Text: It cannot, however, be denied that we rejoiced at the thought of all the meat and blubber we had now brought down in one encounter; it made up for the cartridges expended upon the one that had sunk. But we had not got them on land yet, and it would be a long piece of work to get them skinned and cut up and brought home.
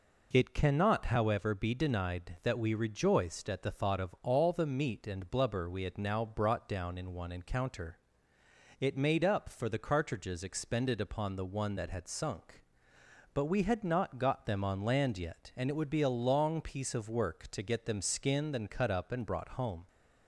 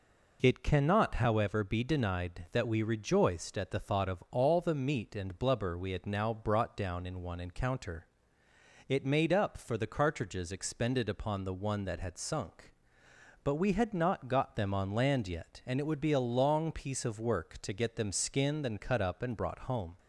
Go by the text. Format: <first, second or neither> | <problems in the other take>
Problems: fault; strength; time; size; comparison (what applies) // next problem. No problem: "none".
neither | none